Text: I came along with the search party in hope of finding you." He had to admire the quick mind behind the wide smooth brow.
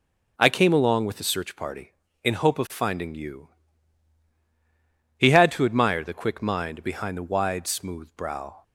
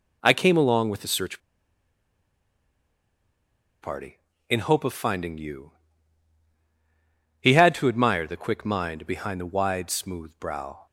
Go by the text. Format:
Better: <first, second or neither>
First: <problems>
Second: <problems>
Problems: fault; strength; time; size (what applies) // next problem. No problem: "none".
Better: first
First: none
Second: pauses between "search" and "party"; strong; at 1.3 s; 2.4 s long